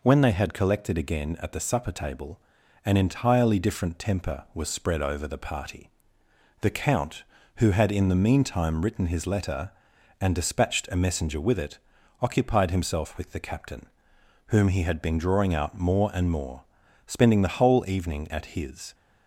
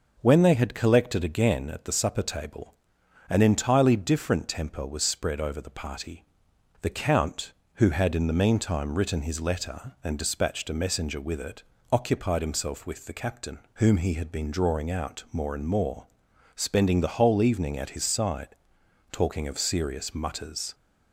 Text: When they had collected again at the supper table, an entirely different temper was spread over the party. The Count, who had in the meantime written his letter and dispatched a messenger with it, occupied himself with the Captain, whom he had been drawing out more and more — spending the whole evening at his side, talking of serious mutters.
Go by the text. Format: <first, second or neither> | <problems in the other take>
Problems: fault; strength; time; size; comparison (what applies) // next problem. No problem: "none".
second | stops before "side talking of serious mutters"; at 18.9 s